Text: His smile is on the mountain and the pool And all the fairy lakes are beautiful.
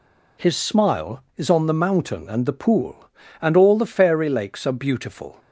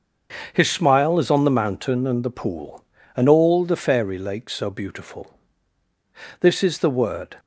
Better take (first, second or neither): first